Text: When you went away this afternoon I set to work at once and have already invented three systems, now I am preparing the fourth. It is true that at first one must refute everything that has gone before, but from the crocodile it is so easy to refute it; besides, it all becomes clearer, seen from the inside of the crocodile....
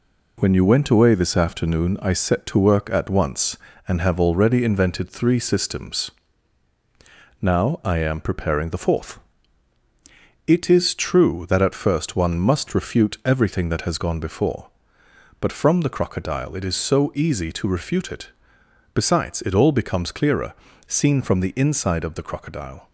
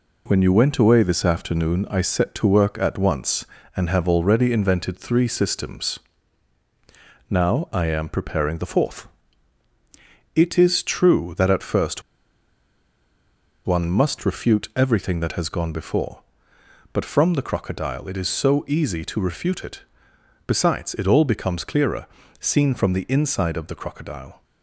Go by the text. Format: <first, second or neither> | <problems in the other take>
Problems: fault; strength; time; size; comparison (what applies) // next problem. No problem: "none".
first | pauses between "first" and "one"; strong; at 12.0 s; 1.6 s long